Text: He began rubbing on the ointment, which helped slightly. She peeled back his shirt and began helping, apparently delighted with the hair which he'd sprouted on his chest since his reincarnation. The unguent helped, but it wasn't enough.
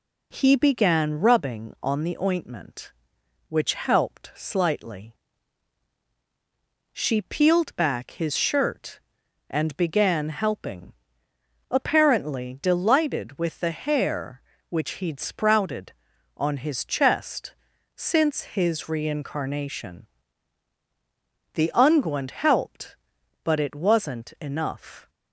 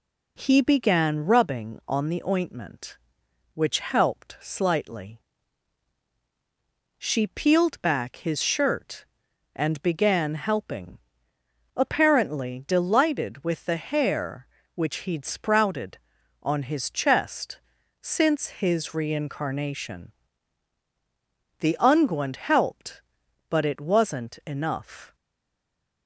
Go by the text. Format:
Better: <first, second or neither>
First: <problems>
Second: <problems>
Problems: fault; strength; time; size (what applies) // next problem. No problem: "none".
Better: first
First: pauses between "chest" and "since"; at 17.5 s; 0.44 s long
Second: pauses between "chest" and "since"; at 17.5 s; 0.44 s long // stays silent after the last word; slight; from 25.1 s on; 0.9 s long